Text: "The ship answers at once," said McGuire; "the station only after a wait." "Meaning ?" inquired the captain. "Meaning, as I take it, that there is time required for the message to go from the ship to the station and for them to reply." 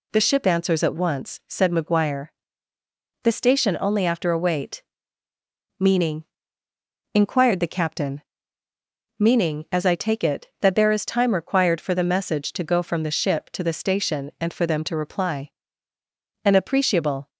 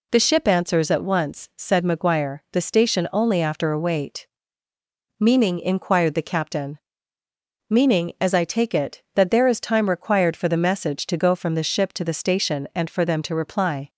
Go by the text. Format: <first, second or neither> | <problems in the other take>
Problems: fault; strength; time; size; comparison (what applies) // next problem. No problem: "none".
second | goes on to say "An appreciable"; noticeable; from 16.4 s on; 0.86 s long